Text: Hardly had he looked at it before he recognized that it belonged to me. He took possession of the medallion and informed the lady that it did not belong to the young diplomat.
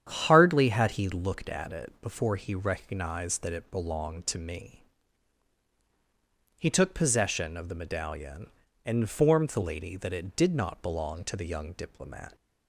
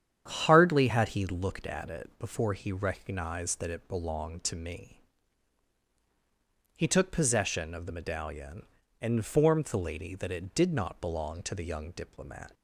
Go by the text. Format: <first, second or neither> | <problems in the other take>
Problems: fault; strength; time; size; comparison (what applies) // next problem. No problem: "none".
neither | starts louder than the rest; strong; the same in both